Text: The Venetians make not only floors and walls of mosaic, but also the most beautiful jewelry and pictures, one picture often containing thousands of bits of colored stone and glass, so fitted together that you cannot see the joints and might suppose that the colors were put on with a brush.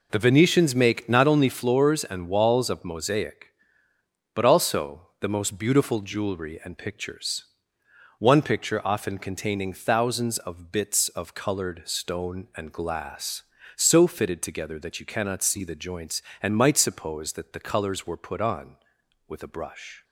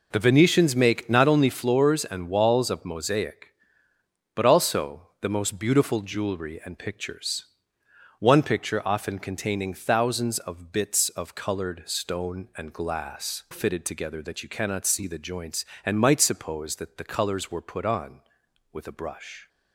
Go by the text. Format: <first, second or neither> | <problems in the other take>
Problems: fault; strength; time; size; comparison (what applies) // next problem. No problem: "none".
first | skips "so"; at 13.4 s